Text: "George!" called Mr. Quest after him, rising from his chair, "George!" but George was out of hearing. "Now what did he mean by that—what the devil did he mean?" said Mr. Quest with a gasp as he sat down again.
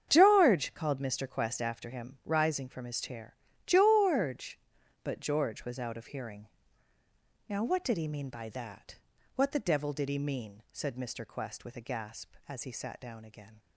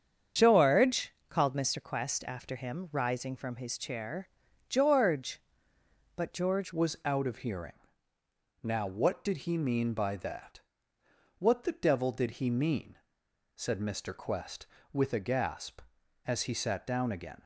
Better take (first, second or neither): first